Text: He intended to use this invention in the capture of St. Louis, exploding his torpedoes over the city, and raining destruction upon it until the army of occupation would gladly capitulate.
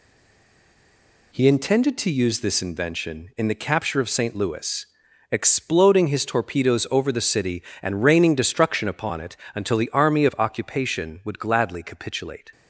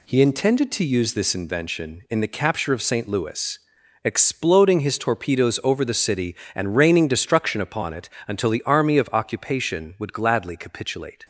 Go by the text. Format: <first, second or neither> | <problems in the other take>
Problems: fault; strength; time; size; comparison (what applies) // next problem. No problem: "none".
second | stays silent before the first word; noticeable; until 1.3 s; 1.3 s long // pauses between "it" and "until"; slight; at 9.3 s; 0.20 s long; slight in the second